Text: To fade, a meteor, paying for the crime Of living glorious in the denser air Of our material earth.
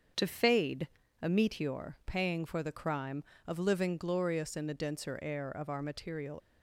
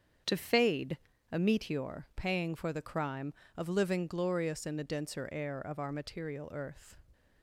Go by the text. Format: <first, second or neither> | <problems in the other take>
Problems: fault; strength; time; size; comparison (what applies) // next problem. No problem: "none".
second | starts louder than the rest; until 1.4 s; 7 dB; strong in the second // stops before "earth"; at 6.4 s